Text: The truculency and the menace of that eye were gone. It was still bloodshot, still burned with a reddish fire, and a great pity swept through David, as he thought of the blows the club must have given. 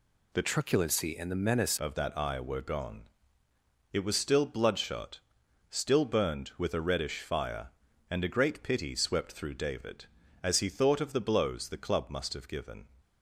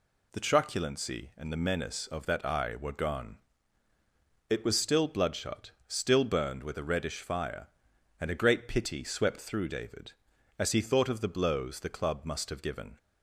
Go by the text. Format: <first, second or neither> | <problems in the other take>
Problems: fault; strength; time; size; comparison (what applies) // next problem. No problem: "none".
second | changes voice from "truculency" to "menace"; from 0.4 to 1.7 s; 1.3 s long